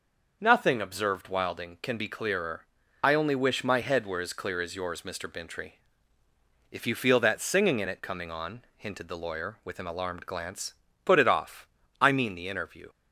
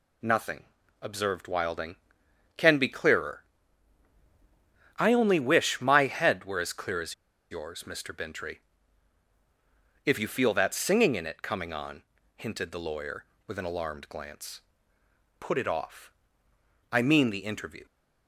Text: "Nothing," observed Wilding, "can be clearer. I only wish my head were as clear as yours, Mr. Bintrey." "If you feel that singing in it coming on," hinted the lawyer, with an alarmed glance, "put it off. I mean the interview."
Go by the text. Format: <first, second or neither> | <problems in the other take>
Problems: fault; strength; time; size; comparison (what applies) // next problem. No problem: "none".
first | pauses between "as" and "yours"; at 7.1 s; 0.37 s long